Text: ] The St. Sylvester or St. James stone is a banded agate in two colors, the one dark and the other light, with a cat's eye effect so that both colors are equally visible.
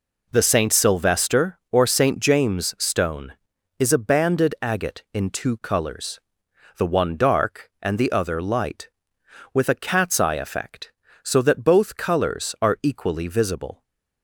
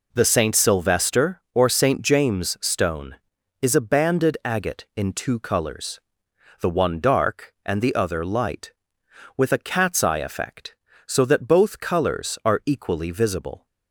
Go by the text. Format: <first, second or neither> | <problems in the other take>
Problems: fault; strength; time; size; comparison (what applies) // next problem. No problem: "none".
neither | none